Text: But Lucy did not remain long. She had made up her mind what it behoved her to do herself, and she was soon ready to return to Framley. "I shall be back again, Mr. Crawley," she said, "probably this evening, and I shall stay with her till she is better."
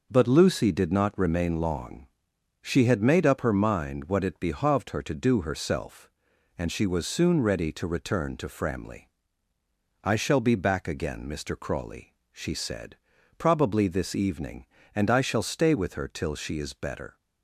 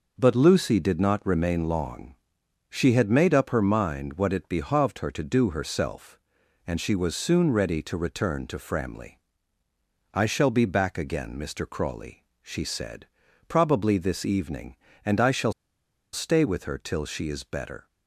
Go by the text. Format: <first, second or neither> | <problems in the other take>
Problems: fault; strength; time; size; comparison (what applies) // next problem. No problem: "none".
first | pauses between "shall" and "stay"; noticeable; at 15.5 s; 0.60 s long